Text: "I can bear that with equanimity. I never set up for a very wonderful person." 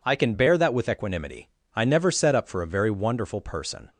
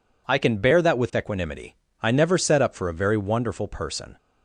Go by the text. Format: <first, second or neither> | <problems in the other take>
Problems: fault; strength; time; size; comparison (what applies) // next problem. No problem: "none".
neither | none